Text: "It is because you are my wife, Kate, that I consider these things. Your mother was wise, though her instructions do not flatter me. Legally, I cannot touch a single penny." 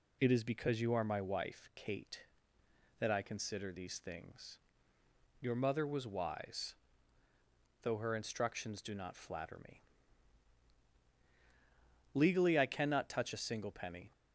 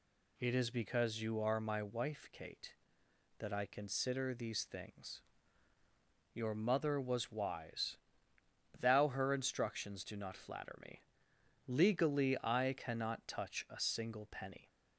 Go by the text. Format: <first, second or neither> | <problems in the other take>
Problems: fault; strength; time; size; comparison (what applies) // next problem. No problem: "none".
first | says "thou" for "though"; at 8.7 s